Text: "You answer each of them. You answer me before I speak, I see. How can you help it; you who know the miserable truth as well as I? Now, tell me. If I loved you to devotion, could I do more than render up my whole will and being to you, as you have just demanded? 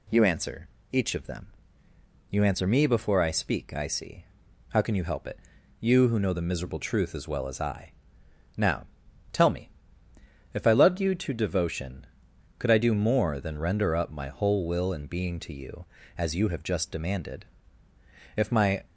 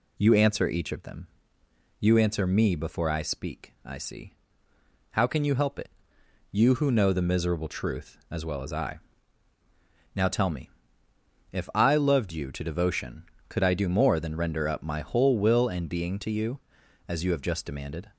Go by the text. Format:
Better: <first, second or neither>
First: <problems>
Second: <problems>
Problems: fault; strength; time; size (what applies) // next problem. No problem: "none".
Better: second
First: pauses between "answer" and "each"; slight; at 0.6 s; 0.22 s long // goes on to say "If my"; from 18.3 s on; 0.50 s long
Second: none